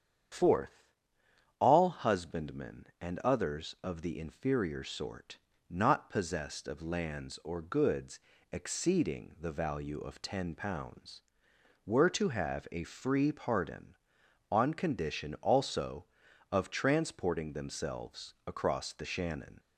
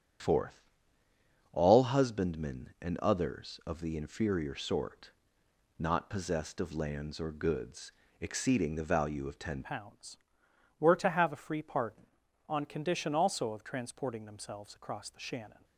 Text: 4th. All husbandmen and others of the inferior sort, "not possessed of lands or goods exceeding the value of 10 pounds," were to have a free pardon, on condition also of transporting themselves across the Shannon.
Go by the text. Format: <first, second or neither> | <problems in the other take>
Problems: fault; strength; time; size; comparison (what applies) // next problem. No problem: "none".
first | starts louder than the rest; strong; until 2.0 s; 9.5 dB; strong in the first // pauses between "goods" and "exceeding"; slight; at 7.9 s; 0.28 s long; slight in the first // changes voice at "pounds"; from 9.6 s on; 6.0 s long